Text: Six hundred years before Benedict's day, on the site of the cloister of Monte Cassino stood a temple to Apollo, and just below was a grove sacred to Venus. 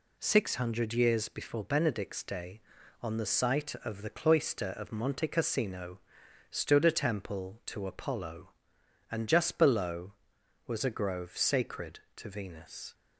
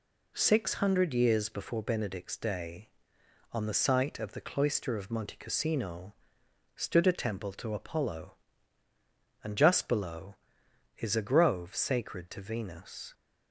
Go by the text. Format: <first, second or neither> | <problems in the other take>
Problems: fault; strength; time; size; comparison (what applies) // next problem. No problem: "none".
first | pauses between "Cassino" and "stood"; noticeable; at 6.1 s; 0.60 s long; noticeable in the first // says "is" for "was"; at 10.9 s